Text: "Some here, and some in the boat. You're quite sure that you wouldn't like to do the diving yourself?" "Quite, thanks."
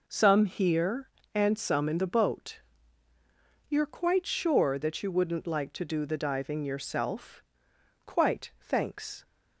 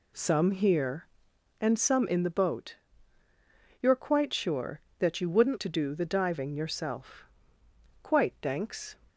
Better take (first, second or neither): first